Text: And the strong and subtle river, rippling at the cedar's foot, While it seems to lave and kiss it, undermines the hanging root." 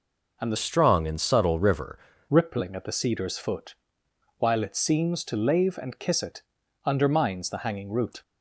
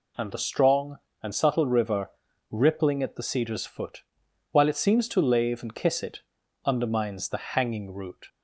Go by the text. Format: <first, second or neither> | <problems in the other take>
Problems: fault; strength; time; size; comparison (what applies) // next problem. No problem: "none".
second | changes voice from "strong" to "river"; from 0.5 to 1.9 s; 1.4 s long